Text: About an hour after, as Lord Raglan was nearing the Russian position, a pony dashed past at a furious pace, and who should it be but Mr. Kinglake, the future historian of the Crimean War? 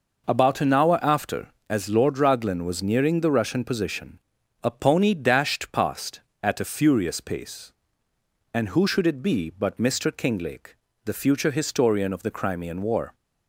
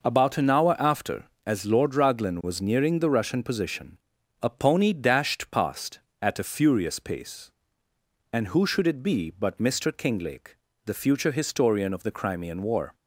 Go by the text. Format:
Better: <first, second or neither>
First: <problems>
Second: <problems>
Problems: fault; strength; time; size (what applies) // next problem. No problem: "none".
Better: neither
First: none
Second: none